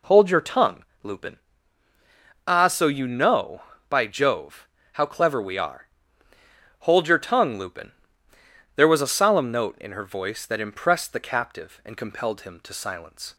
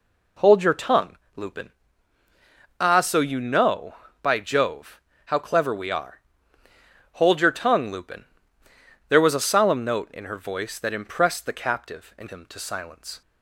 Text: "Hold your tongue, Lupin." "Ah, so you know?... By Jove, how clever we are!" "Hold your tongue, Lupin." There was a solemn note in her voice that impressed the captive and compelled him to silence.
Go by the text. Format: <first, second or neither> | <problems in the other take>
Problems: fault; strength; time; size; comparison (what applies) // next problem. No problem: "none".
first | skips "compelled"; at 12.2 s